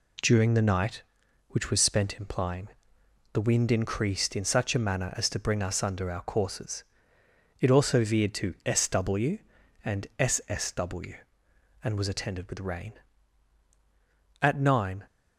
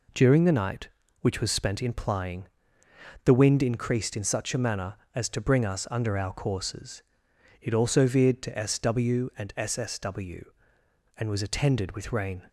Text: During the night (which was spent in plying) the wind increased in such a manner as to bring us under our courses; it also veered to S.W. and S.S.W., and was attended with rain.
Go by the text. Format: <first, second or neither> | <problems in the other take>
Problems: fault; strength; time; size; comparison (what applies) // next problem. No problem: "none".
second | goes on to say "At nine"; noticeable; from 14.4 s on; 0.64 s long